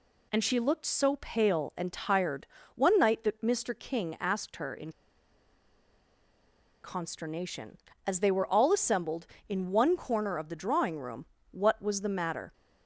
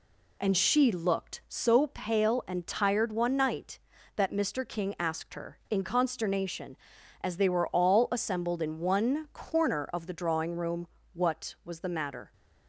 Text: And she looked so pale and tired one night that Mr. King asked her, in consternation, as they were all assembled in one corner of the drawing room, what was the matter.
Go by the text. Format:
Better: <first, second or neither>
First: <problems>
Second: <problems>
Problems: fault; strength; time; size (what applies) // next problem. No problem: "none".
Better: second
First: pauses between "tired" and "one"; slight; at 2.4 s; 0.30 s long // pauses between "in" and "consternation"; strong; at 4.9 s; 1.9 s long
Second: none